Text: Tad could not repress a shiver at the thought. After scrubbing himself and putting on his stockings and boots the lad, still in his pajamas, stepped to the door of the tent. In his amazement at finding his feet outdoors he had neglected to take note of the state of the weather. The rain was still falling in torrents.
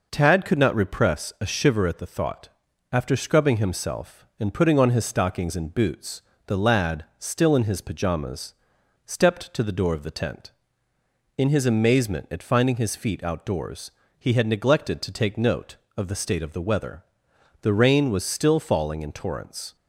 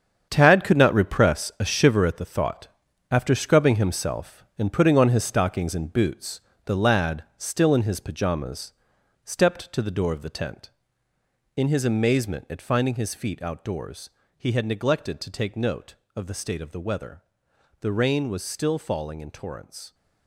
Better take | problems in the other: first | gets quieter; strong; throughout; 11 dB // pauses between "boots" and "the"; slight; at 6.4 s; 0.26 s long; slight in the first // pauses between "outdoors" and "he"; slight; at 14.1 s; 0.26 s long; slight in the first

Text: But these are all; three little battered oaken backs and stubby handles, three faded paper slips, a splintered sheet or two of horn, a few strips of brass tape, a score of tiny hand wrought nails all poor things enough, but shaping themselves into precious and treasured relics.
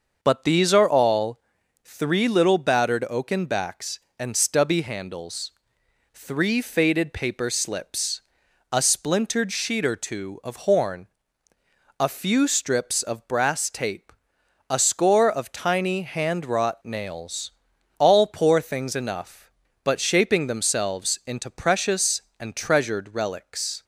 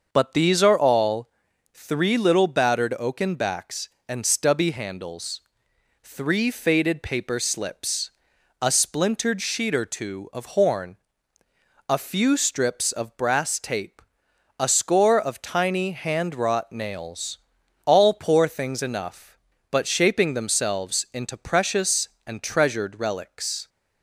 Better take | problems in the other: neither | starts louder than the rest; the same in both // pauses between "nails" and "all"; noticeable; the same in both

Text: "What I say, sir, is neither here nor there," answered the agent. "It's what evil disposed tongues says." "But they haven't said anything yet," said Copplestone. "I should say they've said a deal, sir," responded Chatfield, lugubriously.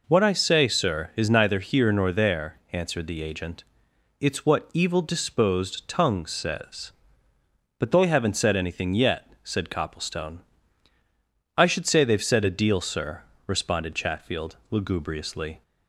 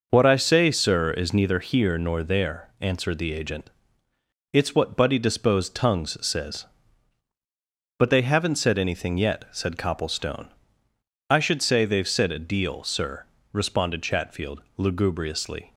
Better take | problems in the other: first | says "buddy" for "evil"; at 4.9 s

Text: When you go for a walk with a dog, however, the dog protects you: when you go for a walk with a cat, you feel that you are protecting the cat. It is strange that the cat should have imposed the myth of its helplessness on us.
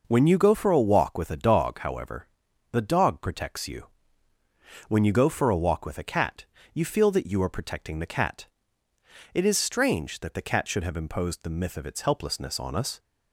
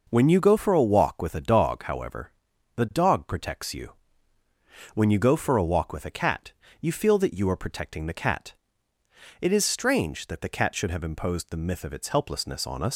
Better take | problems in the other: first | leaves "us" unfinished; at 12.9 s; 105 ms

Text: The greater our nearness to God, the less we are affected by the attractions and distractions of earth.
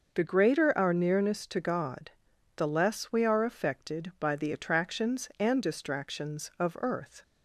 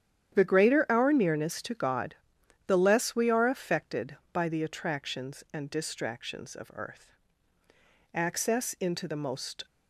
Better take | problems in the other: first | starts louder than the rest; strong; until 1.3 s; 10 dB // goes on to say "Access into the most"; from 8.3 s on; 1.3 s long

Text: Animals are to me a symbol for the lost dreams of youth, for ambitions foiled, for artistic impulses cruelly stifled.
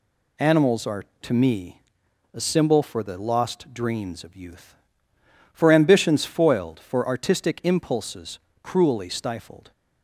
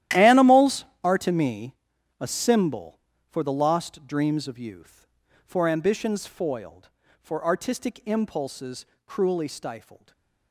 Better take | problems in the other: first | gets quieter; strong; throughout; 15.5 dB // pauses between "me" and "a"; noticeable; at 1.7 s; 0.46 s long; noticeable in the first // pauses between "impulses" and "cruelly"; slight; at 8.8 s; 0.22 s long; slight in the first // stays silent after the last word; slight; from 9.9 s on; 0.6 s long

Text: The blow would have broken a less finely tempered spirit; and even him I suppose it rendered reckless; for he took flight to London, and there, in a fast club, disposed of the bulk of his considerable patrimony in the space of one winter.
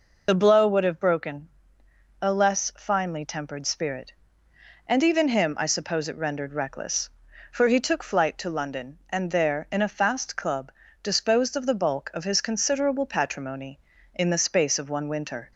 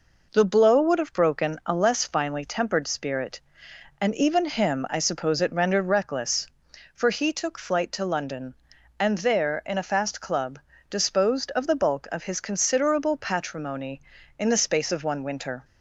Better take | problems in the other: second | loses the start of "The"; at 0.2 s; 35 ms // pauses between "broken" and "a"; noticeable; at 1.4 s; 0.72 s long

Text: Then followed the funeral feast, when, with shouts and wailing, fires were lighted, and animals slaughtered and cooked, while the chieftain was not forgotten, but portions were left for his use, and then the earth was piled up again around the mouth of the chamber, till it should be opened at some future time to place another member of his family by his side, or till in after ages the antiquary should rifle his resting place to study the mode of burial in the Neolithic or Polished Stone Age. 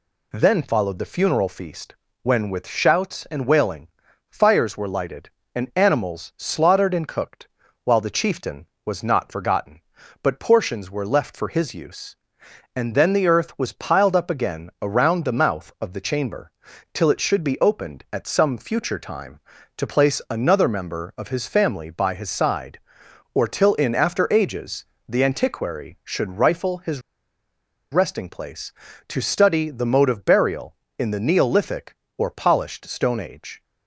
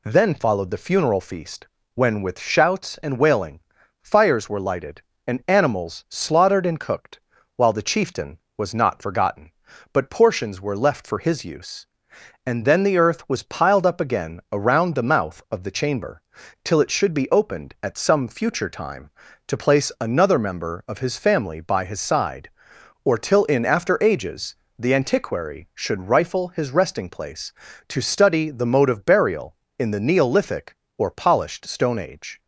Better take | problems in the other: second | pauses between "ages" and "the"; slight; at 24.8 s; 0.20 s long; slight in the second // pauses between "his" and "resting"; noticeable; at 27.0 s; 0.91 s long

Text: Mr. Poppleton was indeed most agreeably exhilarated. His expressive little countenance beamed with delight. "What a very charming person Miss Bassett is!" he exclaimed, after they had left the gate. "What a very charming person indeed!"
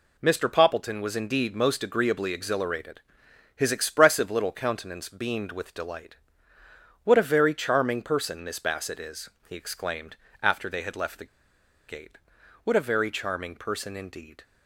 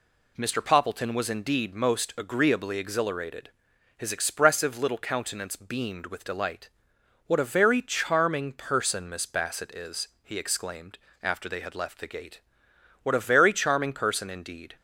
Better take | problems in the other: second | pauses between "the" and "gate"; noticeable; at 11.2 s; 0.62 s long

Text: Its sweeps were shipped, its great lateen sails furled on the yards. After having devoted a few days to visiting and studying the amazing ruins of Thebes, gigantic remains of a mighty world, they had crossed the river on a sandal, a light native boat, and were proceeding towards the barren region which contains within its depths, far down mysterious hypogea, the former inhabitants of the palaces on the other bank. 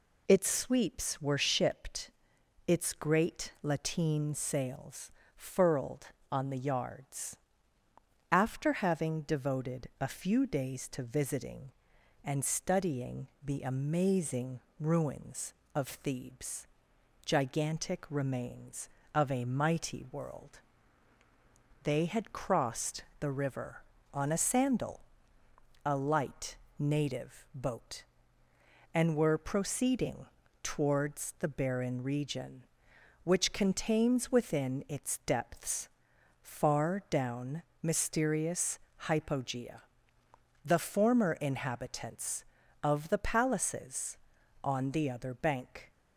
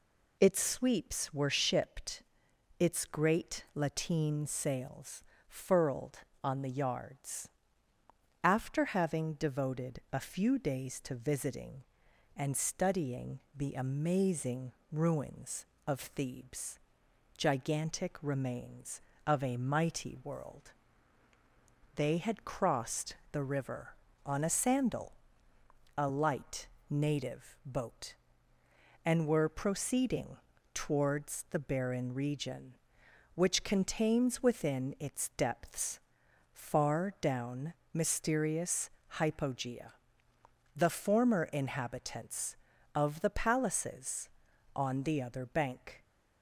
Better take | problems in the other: neither | pauses between "sails" and "furled"; slight; the same in both // pauses between "studying" and "the"; slight; the same in both // pauses between "amazing" and "ruins"; slight; the same in both // pauses between "crossed" and "the"; slight; the same in both // pauses between "light" and "native"; slight; the same in both // pauses between "proceeding" and "towards"; slight; the same in both // pauses between "down" and "mysterious"; slight; the same in both // pauses between "mysterious" and "hypogea"; slight; the same in both

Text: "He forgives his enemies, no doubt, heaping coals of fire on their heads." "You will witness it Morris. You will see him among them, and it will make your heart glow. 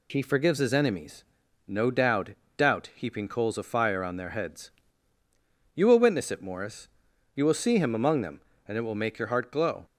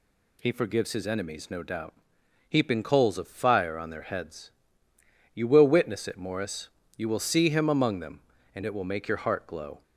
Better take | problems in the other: second | says "doubt" twice; at 2.5 s

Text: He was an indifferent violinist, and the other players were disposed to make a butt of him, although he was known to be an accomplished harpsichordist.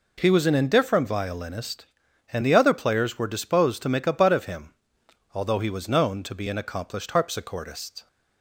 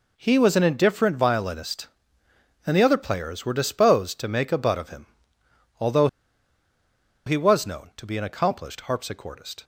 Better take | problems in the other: first | pauses between "although" and "he"; at 6.0 s; 1.1 s long

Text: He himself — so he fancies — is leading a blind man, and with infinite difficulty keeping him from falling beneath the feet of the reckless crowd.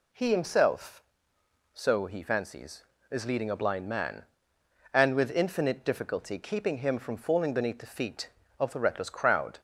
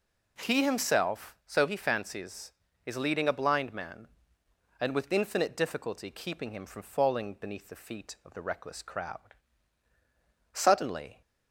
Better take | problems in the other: first | goes on to say "Suddenly"; noticeable; from 10.5 s on; 0.68 s long

